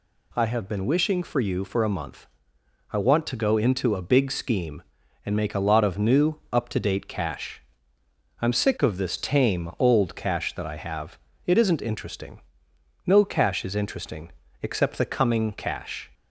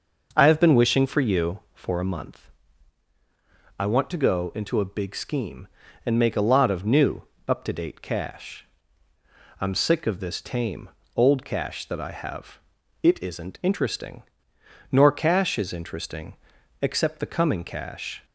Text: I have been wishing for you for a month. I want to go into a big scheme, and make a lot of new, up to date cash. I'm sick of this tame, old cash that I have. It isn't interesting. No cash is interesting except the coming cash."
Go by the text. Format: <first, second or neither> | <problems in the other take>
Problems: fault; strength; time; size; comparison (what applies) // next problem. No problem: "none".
first | says "Nor" for "No"; at 14.9 s // pauses between "interesting" and "except"; noticeable; at 16.3 s; 0.48 s long; slight in the first